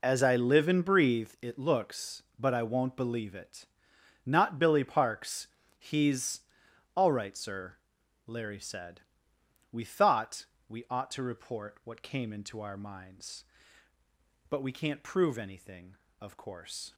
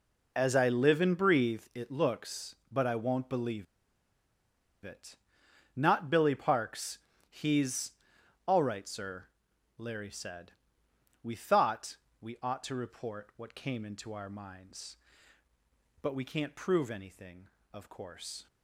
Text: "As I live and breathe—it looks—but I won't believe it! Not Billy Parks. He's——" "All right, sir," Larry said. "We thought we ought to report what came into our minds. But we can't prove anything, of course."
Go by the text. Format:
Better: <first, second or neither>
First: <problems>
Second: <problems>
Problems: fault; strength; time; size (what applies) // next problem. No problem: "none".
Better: first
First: pauses between "thought" and "we"; slight; at 10.4 s; 0.22 s long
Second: pauses between "believe" and "it"; at 3.6 s; 1.1 s long // pauses between "thought" and "we"; slight; at 11.9 s; 0.24 s long